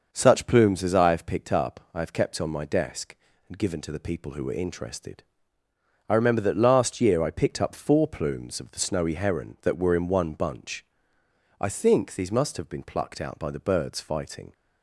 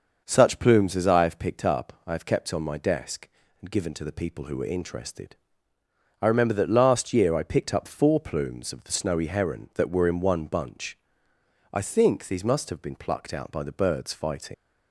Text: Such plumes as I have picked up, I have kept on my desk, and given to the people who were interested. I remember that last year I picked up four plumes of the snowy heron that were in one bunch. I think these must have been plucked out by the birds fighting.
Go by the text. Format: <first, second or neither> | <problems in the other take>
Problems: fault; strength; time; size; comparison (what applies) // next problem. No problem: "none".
first | starts louder than the rest; until 1.2 s; 6 dB; also in the first // leaves "fighting" unfinished; at 14.5 s; 110 ms